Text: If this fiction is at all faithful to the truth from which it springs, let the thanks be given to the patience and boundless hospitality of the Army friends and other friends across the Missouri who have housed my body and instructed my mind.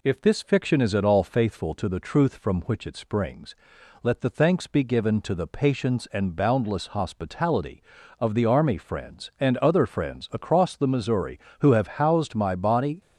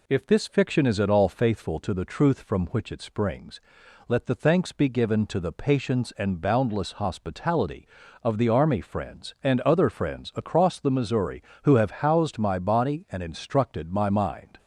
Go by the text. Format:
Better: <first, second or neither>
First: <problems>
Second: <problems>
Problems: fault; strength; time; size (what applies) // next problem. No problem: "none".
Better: second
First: stops before "and instructed my mind"; at 13.0 s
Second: none